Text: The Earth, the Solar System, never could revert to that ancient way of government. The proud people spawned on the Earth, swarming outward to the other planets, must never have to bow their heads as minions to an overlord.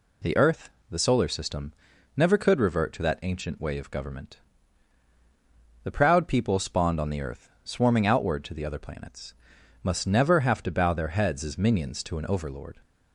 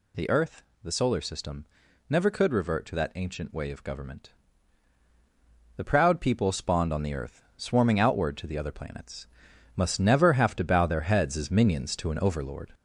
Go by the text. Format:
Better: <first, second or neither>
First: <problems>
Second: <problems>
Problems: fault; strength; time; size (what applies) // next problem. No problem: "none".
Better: first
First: none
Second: gets louder; noticeable; throughout; 4.5 dB